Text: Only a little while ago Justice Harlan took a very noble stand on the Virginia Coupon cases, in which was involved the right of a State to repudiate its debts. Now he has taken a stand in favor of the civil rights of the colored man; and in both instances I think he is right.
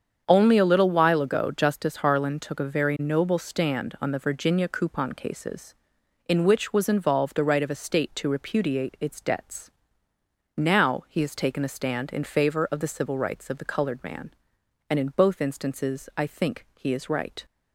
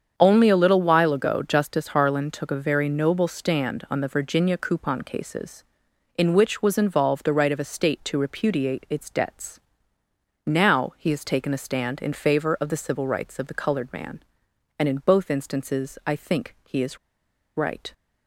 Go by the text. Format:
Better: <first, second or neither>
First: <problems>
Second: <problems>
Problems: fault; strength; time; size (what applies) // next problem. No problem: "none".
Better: first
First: starts louder than the rest; strong; until 1.2 s; 7.5 dB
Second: starts louder than the rest; strong; until 1.1 s; 7.5 dB // pauses between "is" and "right"; noticeable; at 16.9 s; 0.58 s long